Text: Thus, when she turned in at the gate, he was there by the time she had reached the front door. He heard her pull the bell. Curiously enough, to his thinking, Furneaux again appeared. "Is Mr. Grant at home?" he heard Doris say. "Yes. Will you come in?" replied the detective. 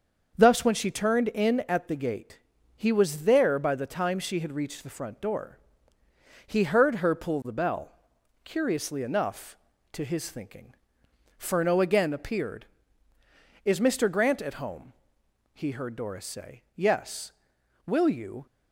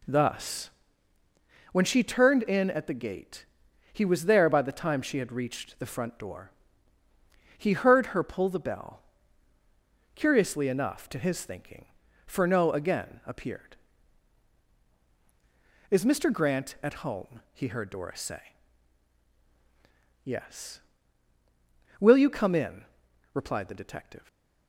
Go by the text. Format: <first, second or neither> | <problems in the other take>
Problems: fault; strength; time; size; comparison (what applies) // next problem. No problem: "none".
second | starts louder than the rest; until 1.4 s; 6.5 dB // stops before "come in replied the detective"; at 18.4 s